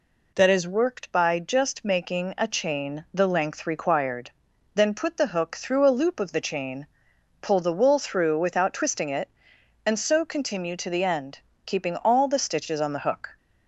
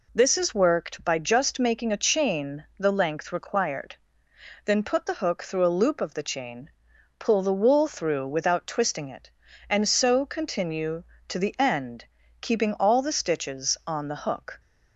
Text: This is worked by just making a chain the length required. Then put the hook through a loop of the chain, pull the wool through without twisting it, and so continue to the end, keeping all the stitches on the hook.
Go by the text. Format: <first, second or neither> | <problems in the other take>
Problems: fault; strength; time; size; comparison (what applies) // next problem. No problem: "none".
second | says "That" for "This"; at 0.3 s